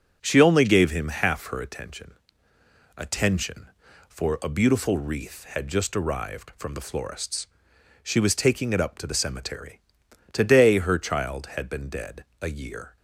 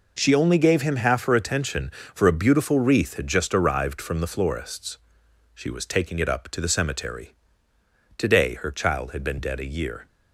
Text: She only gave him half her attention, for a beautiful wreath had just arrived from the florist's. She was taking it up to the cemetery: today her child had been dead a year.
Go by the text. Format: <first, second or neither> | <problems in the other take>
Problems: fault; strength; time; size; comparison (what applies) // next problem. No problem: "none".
second | says "attention" twice; at 2.9 s // pauses between "dead" and "a"; slight; at 12.2 s; 0.16 s long